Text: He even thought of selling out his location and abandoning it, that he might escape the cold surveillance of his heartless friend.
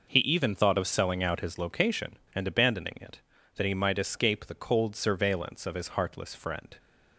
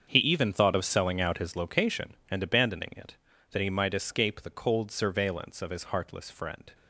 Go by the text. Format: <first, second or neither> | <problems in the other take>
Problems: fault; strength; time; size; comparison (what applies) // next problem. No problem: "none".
first | gets quieter; strong; throughout; 13 dB